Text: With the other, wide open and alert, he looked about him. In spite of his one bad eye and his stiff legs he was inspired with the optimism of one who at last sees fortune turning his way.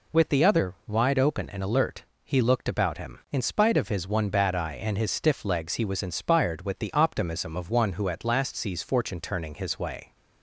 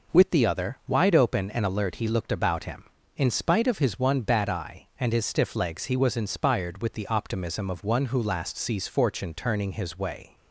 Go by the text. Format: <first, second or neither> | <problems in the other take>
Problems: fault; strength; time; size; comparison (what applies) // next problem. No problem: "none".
first | skips "at"; at 8.2 s